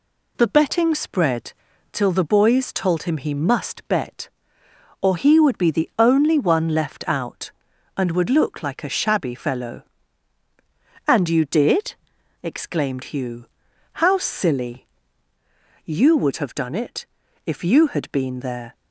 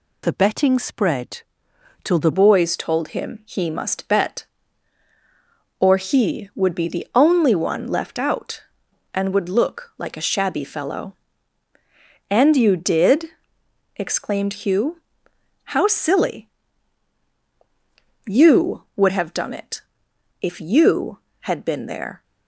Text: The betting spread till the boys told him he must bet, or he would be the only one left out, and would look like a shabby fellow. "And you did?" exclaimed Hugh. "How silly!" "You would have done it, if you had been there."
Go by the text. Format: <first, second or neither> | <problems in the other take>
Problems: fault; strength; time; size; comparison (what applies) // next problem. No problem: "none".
first | pauses between "spread" and "till"; noticeable; at 1.4 s; 0.60 s long; also in the first // changes voice at "boys"; from 2.3 s on; 19.9 s long